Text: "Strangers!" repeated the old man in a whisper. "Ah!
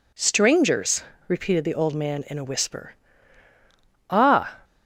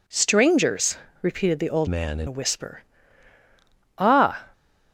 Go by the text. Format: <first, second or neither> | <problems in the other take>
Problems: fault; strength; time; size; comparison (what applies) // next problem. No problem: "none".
first | changes voice from "man" to "in"; from 1.8 to 2.2 s; 0.4 s long